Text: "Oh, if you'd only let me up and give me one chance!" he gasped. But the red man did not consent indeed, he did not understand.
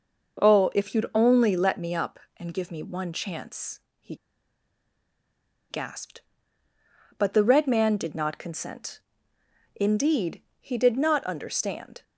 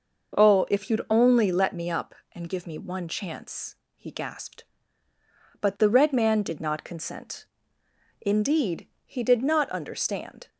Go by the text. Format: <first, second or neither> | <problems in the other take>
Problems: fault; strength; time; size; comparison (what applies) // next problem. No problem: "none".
second | pauses between "he" and "gasped"; strong; at 4.1 s; 1.5 s long // pauses between "consent" and "indeed"; noticeable; at 9.0 s; 0.74 s long; noticeable in the second